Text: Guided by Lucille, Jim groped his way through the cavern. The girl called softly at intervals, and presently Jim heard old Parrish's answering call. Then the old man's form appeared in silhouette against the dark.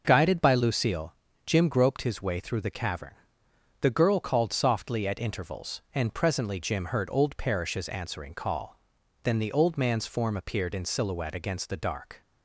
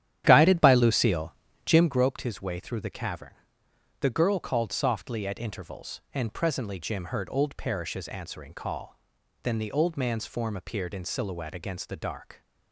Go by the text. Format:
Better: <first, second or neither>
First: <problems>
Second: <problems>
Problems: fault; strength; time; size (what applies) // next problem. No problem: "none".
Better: first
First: none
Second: starts louder than the rest; strong; until 1.9 s; 10.5 dB